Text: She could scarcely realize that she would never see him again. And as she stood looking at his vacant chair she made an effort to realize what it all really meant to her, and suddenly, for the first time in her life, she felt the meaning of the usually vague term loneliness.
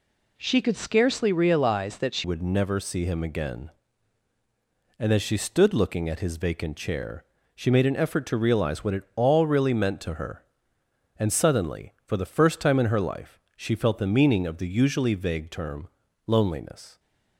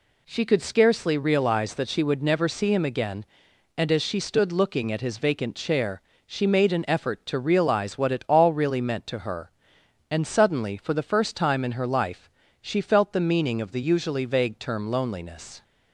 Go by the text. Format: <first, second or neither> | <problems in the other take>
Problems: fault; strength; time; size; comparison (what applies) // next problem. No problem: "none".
second | changes voice at "would"; from 2.2 s on; 14.7 s long // pauses between "chair" and "she"; slight; at 7.2 s; 0.32 s long; slight in the second // pauses between "term" and "loneliness"; at 15.8 s; 0.40 s long